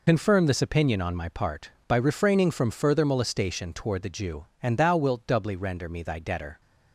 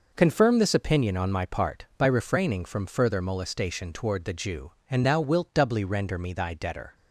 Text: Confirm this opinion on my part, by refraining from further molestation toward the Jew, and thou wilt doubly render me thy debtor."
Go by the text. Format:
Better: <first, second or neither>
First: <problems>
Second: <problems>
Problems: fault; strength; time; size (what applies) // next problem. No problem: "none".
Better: second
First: loses the start of "Confirm"; at 0.0 s; 55 ms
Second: none